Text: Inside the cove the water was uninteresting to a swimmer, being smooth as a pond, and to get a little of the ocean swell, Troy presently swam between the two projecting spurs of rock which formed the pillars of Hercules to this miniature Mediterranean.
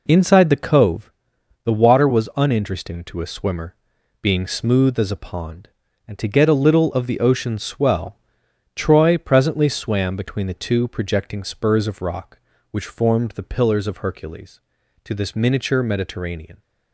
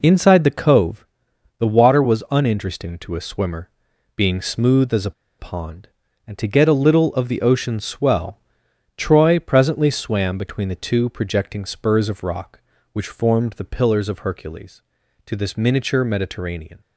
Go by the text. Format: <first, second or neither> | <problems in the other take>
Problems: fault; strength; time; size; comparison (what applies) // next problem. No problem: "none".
first | pauses between "cove" and "the"; noticeable; at 1.0 s; 0.54 s long; noticeable in the first // pauses between "a" and "pond"; slight; at 5.1 s; 0.27 s long